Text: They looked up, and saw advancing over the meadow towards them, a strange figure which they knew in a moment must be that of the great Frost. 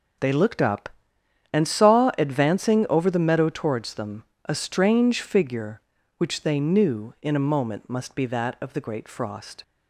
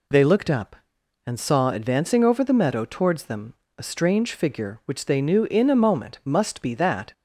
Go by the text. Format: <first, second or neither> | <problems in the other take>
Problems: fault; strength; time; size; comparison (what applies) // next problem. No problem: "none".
first | stops before "of the great Frost"; at 7.1 s